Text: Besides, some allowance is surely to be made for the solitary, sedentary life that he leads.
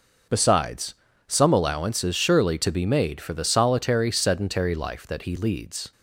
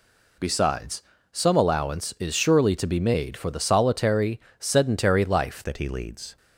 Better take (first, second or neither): first